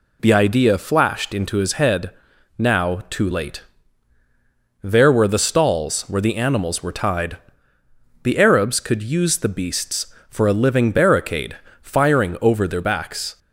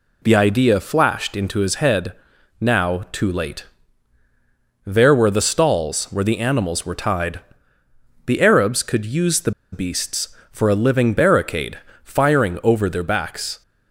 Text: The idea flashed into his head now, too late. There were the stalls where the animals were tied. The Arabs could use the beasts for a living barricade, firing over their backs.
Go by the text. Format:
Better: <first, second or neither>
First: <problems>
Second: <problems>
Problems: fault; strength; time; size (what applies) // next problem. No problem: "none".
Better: first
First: pauses between "head" and "now"; noticeable; at 2.1 s; 0.48 s long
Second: pauses between "head" and "now"; noticeable; at 2.1 s; 0.48 s long // pauses between "the" and "beasts"; slight; at 9.5 s; 0.21 s long